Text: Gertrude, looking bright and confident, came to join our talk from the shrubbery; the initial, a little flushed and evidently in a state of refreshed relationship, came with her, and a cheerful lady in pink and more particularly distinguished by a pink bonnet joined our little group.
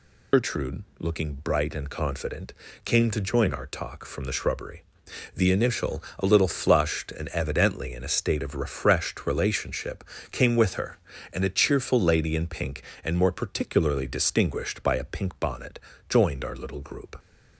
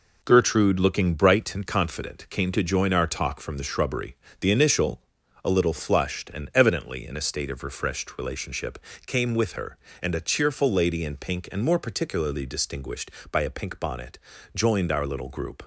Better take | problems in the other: second | loses the start of "Gertrude"; at 0.3 s; 105 ms // pauses between "bonnet" and "joined"; slight; at 15.7 s; 0.28 s long; slight in the second

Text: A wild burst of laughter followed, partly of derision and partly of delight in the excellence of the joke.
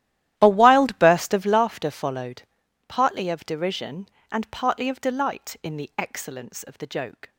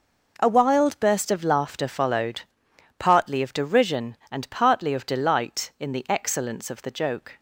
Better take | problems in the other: second | starts louder than the rest; strong; until 1.6 s; 13 dB

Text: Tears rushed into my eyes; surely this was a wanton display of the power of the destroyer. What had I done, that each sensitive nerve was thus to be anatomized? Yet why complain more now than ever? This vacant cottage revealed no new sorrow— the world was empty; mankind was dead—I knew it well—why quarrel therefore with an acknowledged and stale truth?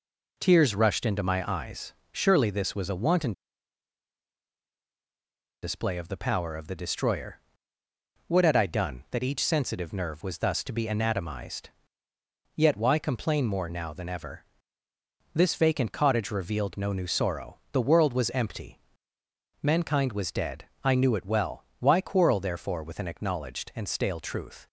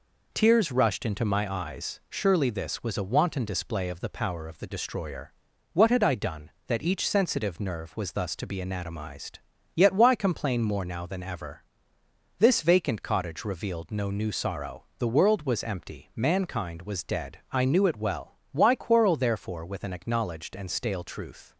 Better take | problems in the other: second | pauses between "wanton" and "display"; strong; at 3.3 s; 2.2 s long

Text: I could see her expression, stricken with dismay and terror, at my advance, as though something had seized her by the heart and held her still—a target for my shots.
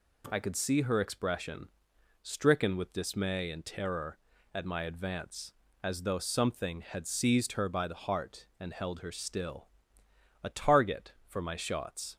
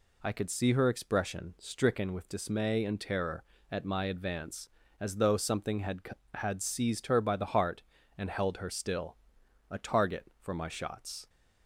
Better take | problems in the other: first | says "had" twice; at 6.3 s

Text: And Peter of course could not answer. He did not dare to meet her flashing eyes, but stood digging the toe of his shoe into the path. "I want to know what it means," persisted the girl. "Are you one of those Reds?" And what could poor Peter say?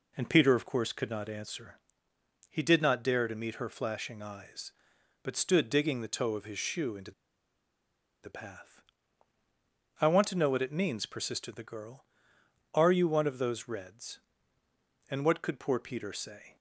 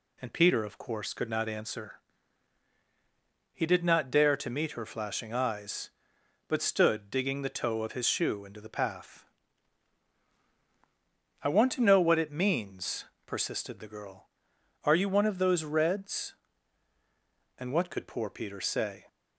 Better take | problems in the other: second | pauses between "into" and "the"; at 7.1 s; 1.1 s long

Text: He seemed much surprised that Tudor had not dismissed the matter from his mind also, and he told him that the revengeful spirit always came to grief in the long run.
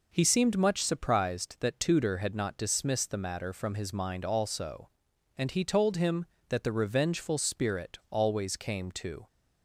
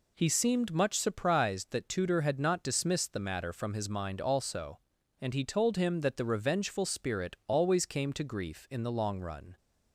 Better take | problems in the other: second | stops before "grief in the long run"; at 9.2 s

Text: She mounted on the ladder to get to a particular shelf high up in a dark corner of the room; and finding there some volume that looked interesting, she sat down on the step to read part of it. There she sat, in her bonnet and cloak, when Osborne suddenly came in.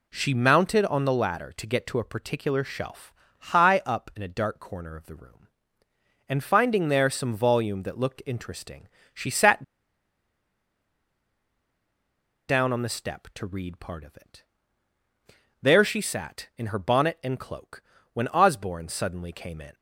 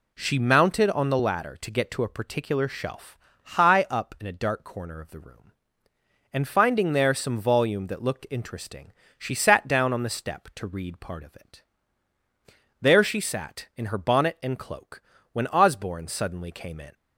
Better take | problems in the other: second | pauses between "shelf" and "high"; slight; at 3.1 s; 0.28 s long; slight in the second // pauses between "sat" and "down"; strong; at 9.6 s; 2.8 s long

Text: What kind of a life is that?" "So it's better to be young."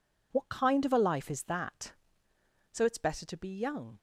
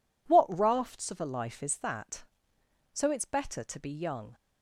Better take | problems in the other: first | says "rafts" for "kind"; at 0.5 s

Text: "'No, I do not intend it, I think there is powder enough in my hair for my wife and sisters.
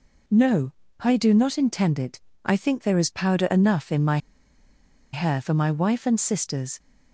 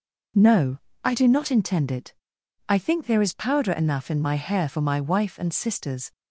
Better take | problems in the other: second | pauses between "my" and "hair"; noticeable; at 4.1 s; 0.95 s long

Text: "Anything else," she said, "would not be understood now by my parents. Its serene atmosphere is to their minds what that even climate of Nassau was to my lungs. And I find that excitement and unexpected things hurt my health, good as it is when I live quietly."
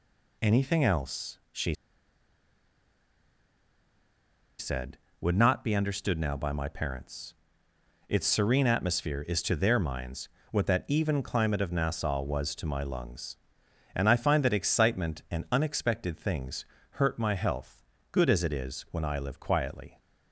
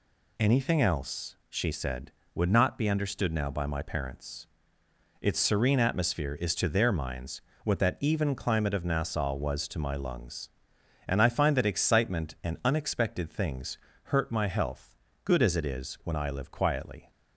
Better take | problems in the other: second | pauses between "she" and "said"; strong; at 1.7 s; 2.8 s long // pauses between "minds" and "what"; slight; at 10.2 s; 0.22 s long; slight in the second // pauses between "things" and "hurt"; slight; at 16.6 s; 0.26 s long; slight in the second

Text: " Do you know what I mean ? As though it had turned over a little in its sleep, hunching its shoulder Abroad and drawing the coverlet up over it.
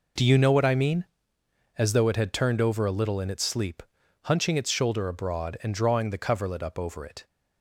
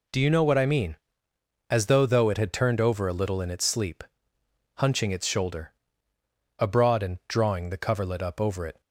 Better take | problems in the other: first | says "though" twice; at 2.0 s // pauses between "shoulder" and "Abroad"; noticeable; at 5.7 s; 0.84 s long

